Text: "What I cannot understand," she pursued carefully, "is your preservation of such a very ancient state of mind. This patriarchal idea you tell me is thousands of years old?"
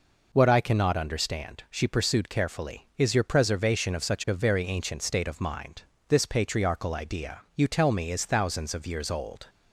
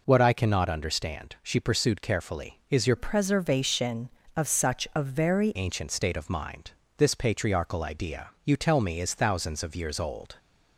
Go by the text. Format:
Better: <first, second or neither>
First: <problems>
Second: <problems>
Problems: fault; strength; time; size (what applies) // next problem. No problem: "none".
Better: first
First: pauses between "idea" and "you"; slight; at 7.3 s; 0.16 s long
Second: changes voice from "preservation" to "very"; from 2.9 to 5.5 s; 2.6 s long // pauses between "idea" and "you"; slight; at 8.2 s; 0.16 s long